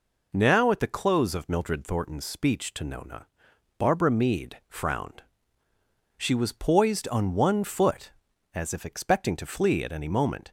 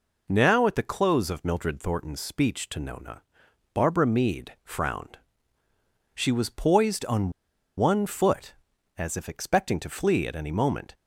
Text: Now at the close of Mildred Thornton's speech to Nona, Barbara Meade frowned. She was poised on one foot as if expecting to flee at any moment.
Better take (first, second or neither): first